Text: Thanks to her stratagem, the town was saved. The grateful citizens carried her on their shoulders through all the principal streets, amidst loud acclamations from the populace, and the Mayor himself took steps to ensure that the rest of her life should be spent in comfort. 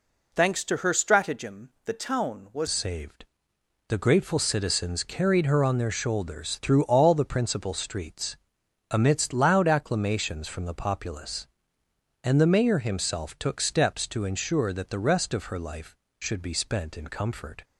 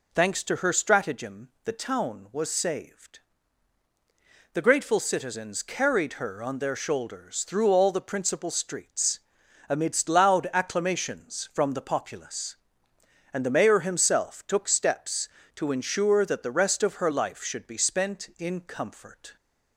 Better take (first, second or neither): second